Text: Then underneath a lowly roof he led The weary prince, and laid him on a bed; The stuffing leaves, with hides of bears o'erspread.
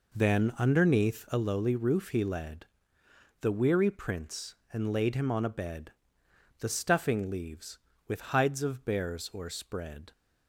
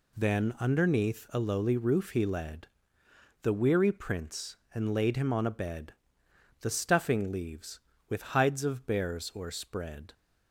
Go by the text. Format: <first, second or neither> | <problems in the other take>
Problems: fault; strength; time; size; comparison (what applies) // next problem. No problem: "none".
second | starts louder than the rest; noticeable; until 1.5 s; 4 dB // pauses between "led" and "The"; noticeable; at 2.6 s; 0.74 s long; noticeable in the second